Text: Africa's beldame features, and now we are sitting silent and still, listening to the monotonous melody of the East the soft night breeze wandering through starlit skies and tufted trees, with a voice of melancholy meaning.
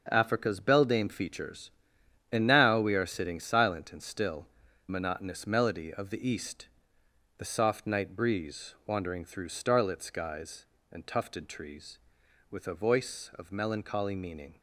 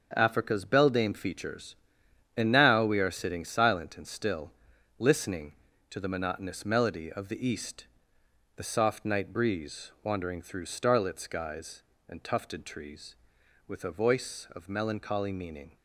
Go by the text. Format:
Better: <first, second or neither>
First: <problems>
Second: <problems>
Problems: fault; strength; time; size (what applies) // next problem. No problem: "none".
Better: second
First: starts louder than the rest; until 1.1 s; 6.5 dB // skips "listening to the"; at 4.6 s // pauses between "East" and "the"; noticeable; at 6.6 s; 0.72 s long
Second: starts louder than the rest; until 1.1 s; 6.5 dB // pauses between "East" and "the"; noticeable; at 7.8 s; 0.72 s long